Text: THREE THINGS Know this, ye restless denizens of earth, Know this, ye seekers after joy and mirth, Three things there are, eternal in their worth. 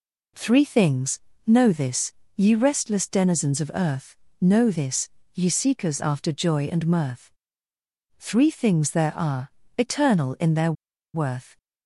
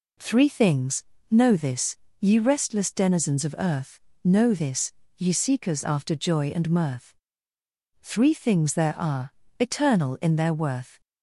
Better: second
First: pauses between "THINGS" and "Know"; slight; at 1.2 s; 0.26 s long // pauses between "their" and "worth"; at 10.7 s; 0.41 s long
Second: pauses between "THINGS" and "Know"; slight; at 1.0 s; 0.26 s long

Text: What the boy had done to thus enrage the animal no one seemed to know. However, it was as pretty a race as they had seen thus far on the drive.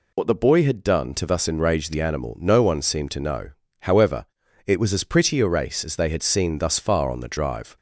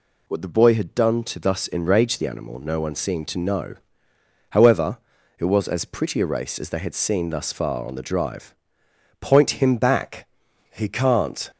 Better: first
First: none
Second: goes on to say "Point him back He can't"; strong; from 9.2 s on; 2.3 s long

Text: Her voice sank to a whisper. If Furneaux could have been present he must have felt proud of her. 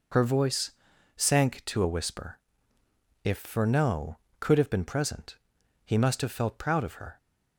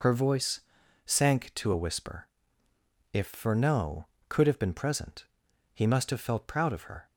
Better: neither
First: pauses between "voice" and "sank"; at 0.7 s; 0.44 s long // pauses between "present" and "he"; noticeable; at 5.3 s; 0.48 s long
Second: pauses between "voice" and "sank"; at 0.6 s; 0.44 s long // pauses between "present" and "he"; noticeable; at 5.2 s; 0.48 s long

